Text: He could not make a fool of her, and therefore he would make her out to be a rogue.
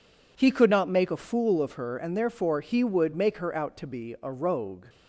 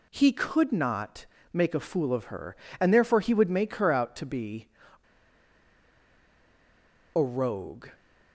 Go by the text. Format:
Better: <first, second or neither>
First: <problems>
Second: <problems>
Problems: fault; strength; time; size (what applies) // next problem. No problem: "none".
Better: first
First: none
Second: pauses between "not" and "make"; slight; at 1.2 s; 0.26 s long // pauses between "be" and "a"; strong; at 4.6 s; 2.4 s long